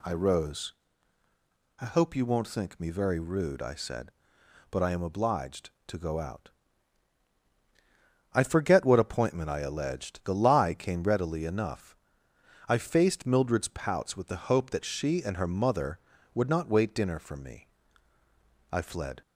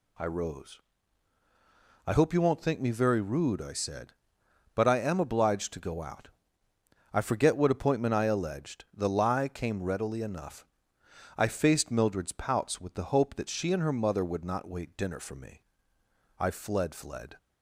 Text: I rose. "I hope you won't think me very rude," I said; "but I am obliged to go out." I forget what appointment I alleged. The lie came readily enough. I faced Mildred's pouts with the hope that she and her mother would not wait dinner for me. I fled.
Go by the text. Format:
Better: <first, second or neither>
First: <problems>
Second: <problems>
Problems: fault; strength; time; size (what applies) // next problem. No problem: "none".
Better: first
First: none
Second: says "fled" twice; at 16.9 s